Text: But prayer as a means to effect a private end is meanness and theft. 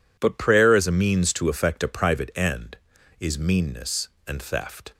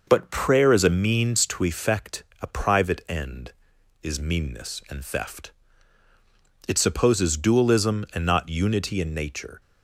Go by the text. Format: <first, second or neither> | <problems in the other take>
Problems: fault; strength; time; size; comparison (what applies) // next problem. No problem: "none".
first | pauses between "effect" and "a"; slight; at 2.2 s; 0.18 s long // goes on to say "It supposes dualism and not unity in nature"; strong; from 6.6 s on; 2.9 s long